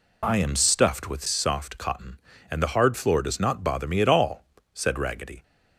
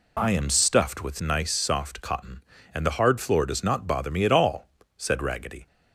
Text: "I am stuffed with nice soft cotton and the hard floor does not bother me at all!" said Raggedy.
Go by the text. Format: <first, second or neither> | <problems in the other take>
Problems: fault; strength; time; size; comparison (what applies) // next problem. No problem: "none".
second | skips "nice"; at 1.2 s